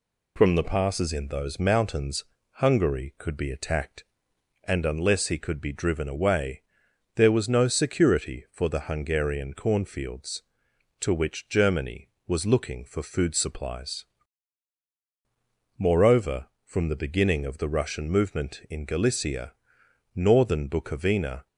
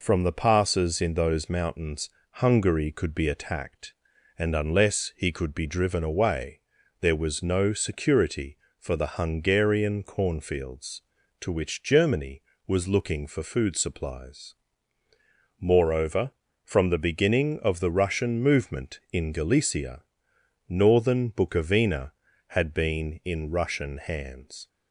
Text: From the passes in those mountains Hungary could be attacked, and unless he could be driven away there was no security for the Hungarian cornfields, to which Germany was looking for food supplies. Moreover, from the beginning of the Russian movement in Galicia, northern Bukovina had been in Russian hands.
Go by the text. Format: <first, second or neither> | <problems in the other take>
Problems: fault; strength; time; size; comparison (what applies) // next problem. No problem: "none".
second | pauses between "mountains" and "Hungary"; slight; at 2.2 s; 0.34 s long; slight in the second // pauses between "away" and "there"; noticeable; at 6.6 s; 0.54 s long; also in the second // stops before "had been in Russian hands"; at 21.4 s